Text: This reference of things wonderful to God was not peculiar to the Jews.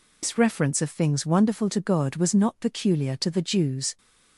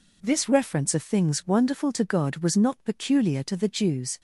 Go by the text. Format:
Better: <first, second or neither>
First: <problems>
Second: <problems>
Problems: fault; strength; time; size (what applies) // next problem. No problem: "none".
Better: second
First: loses the start of "This"; at 0.2 s; 115 ms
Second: none